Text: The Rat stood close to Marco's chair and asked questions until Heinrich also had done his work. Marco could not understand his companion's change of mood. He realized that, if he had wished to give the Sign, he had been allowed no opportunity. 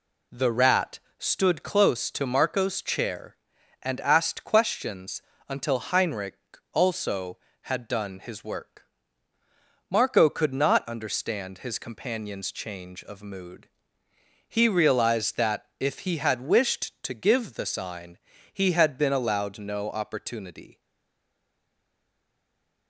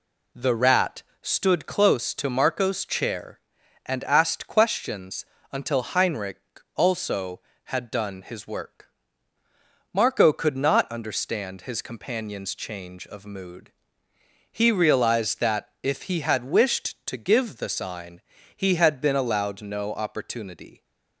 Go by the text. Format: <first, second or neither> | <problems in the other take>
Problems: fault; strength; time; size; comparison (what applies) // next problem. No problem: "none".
second | pauses between "Rat" and "stood"; slight; at 0.9 s; 0.20 s long; slight in the second // pauses between "questions" and "until"; slight; at 5.2 s; 0.26 s long; slight in the second // pauses between "Heinrich" and "also"; slight; at 6.3 s; 0.34 s long; slight in the second // stays silent after the last word; from 20.7 s on; 2.1 s long